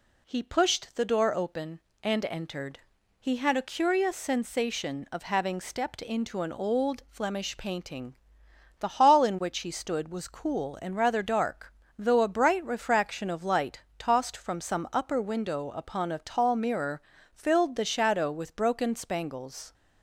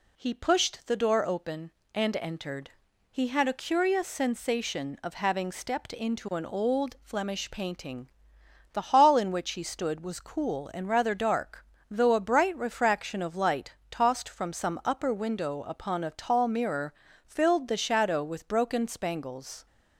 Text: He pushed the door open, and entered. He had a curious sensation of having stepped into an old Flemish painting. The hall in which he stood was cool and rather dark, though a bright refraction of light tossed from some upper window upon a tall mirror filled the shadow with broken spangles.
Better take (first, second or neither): neither